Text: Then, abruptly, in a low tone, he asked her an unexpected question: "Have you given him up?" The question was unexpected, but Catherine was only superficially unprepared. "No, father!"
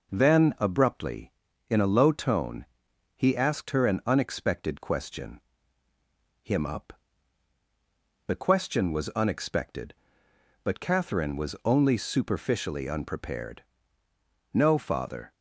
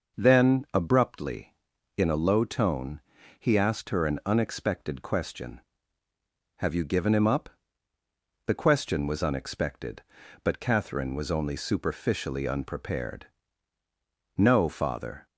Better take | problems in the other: second | skips "Have you given"; at 5.8 s

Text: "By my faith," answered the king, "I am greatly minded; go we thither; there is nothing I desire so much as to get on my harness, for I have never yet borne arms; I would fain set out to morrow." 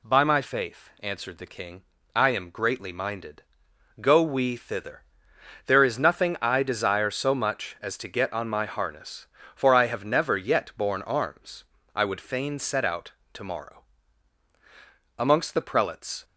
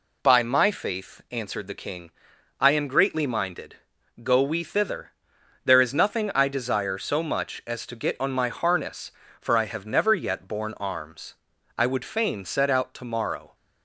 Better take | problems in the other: second | goes on to say "Amongst the prelates"; noticeable; from 15.2 s on; 1.0 s long

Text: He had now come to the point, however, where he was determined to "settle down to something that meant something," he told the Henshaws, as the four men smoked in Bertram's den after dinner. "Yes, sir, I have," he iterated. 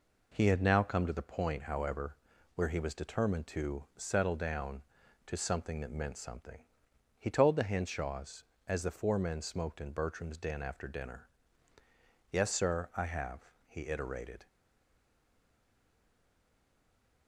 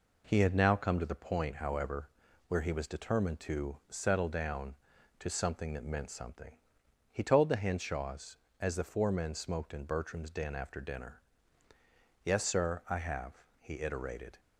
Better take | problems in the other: second | stays silent after the last word; strong; from 14.4 s on; 2.8 s long

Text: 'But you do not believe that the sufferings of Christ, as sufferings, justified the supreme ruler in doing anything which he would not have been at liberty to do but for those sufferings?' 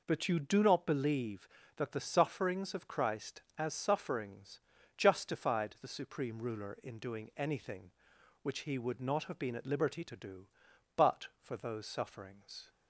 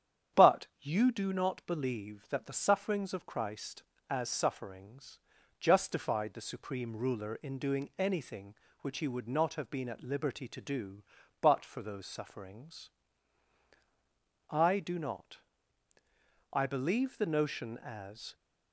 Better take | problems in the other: first | starts louder than the rest; strong; until 1.4 s; 9 dB // goes on to say "I do not I believe the notion as"; strong; from 14.5 s on; 3.8 s long

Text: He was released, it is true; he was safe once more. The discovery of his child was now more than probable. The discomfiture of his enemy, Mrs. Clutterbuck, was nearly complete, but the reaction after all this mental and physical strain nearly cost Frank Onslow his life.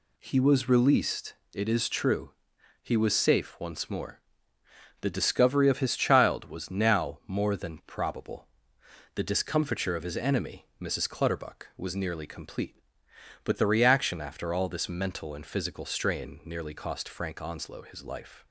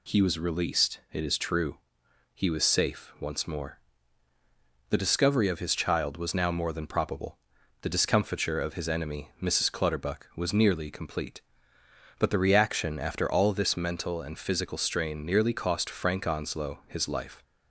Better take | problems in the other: neither | none

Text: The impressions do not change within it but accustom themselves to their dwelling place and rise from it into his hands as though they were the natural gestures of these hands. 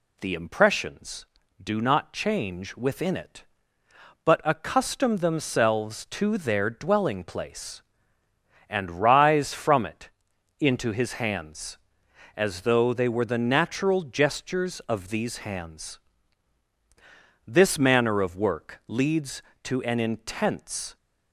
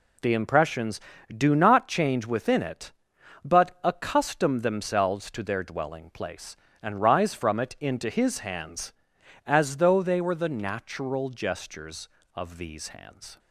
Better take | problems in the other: second | pauses between "it" and "into"; noticeable; at 10.0 s; 0.50 s long // goes on to say "This manner of work leads to an intense"; strong; from 17.4 s on; 3.5 s long

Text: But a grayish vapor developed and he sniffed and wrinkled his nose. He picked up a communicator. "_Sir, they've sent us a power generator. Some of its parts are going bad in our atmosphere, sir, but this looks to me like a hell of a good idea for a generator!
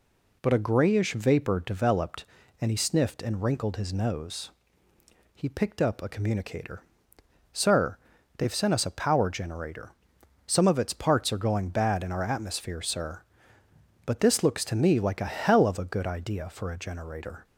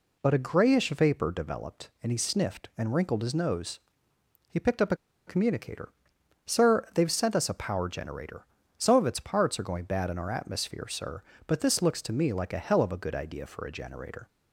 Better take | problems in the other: first | pauses between "a" and "communicator"; slight; at 4.9 s; 0.30 s long

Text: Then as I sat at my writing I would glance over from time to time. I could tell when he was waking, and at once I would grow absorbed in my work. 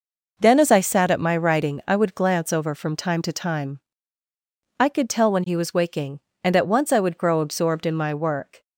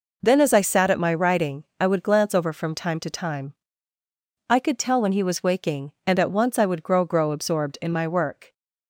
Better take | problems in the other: first | says "grow" twice; at 7.0 s

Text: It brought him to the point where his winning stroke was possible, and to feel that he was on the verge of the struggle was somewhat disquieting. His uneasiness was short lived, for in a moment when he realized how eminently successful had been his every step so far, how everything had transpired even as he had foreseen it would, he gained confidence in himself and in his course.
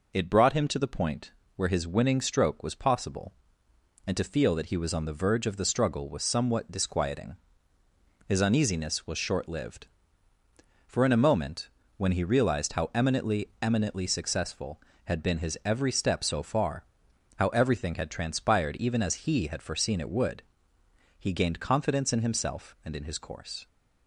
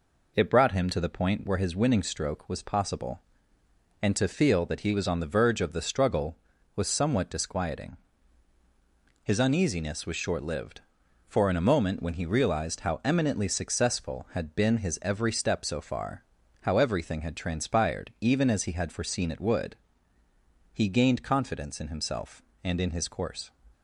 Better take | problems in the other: second | pauses between "point" and "where"; slight; at 1.3 s; 0.24 s long // pauses between "moment" and "when"; slight; at 11.6 s; 0.30 s long // says "eminently" twice; at 13.6 s

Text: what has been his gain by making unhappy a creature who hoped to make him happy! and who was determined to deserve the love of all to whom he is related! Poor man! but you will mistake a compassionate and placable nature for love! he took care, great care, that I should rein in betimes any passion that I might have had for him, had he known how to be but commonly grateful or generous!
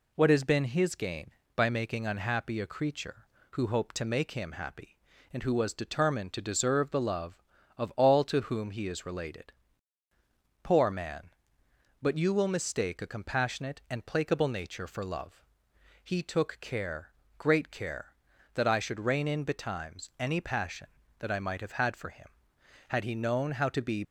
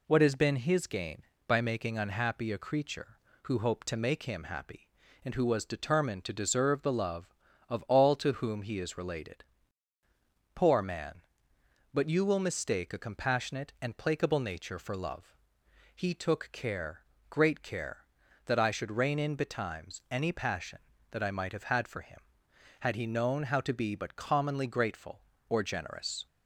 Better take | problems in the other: second | stops before "but commonly grateful or generous"; at 24.0 s

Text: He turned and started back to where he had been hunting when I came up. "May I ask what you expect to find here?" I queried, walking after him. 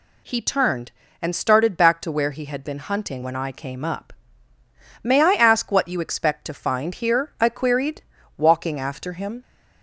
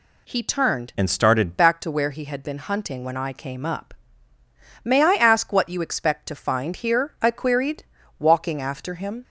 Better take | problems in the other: first | changes voice from "and" to "started"; from 0.9 to 1.5 s; 0.6 s long

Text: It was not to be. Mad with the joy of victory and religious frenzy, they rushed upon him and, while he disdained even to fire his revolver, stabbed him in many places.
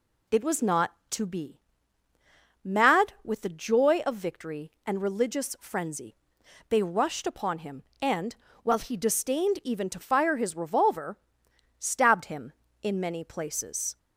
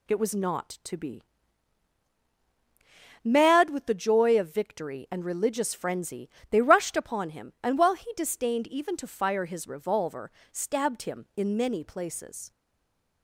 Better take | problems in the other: first | stays silent after the last word; slight; from 12.5 s on; 0.7 s long

